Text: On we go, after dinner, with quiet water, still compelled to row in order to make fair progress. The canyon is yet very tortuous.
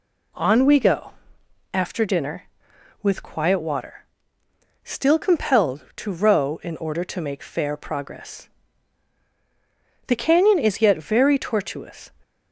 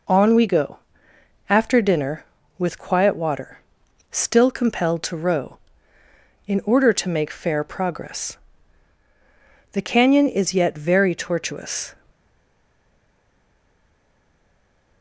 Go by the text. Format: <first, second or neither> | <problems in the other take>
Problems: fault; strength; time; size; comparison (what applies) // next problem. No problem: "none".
first | stays silent after the last word; strong; from 12.1 s on; 2.9 s long